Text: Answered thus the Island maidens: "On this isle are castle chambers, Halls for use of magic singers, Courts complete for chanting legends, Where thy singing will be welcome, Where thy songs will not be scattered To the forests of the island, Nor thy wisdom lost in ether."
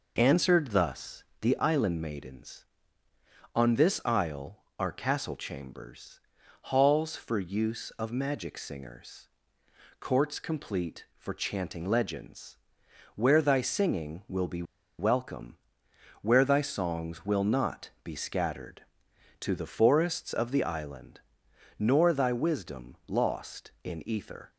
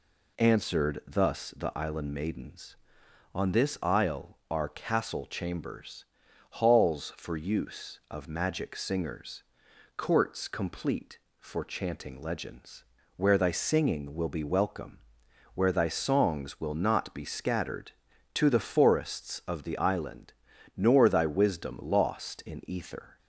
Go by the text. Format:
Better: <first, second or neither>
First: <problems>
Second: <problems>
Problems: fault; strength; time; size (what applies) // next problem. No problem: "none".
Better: second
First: pauses between "thus" and "the"; slight; at 1.2 s; 0.18 s long // pauses between "be" and "welcome"; slight; at 14.6 s; 0.35 s long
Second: none